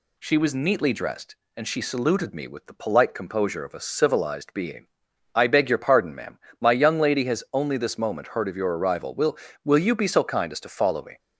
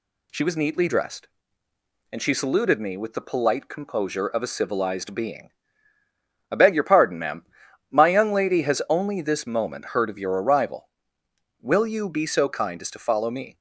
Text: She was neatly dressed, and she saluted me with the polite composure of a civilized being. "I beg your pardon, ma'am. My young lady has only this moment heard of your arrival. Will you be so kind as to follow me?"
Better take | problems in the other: second | says "Will" twice; at 9.6 s

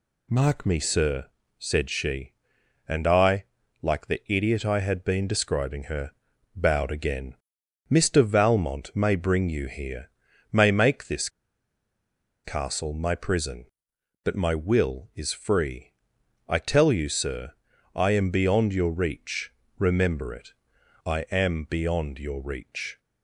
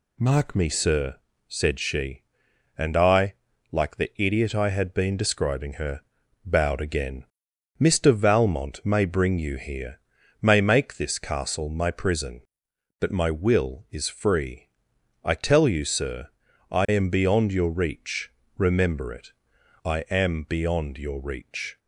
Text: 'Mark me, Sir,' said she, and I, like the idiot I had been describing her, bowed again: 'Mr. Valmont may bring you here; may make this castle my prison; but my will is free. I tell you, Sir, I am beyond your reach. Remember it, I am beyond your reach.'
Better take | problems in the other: second | pauses between "this" and "castle"; at 11.2 s; 1.1 s long

